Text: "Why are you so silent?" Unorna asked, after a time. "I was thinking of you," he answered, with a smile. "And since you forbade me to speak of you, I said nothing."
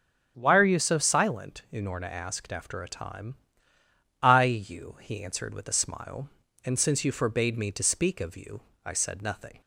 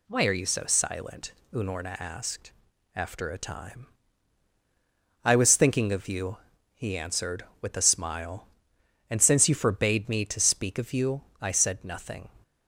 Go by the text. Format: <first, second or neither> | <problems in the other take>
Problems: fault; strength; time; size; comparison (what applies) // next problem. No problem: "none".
second | starts louder than the rest; strong; until 1.3 s; 7.5 dB // skips "was thinking of"; at 4.4 s